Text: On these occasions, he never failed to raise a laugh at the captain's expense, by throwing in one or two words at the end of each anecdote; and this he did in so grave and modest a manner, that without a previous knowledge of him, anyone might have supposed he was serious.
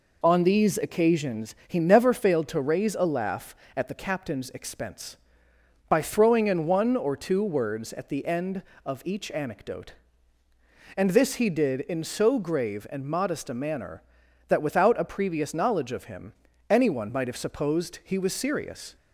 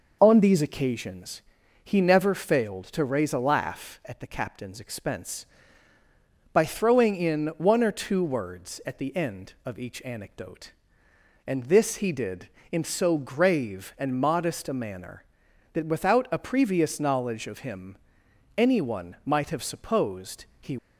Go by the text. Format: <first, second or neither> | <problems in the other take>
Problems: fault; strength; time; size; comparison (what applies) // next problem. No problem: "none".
first | pauses between "supposed" and "he"; slight; at 20.4 s; 0.16 s long // stops before "was serious"; at 20.7 s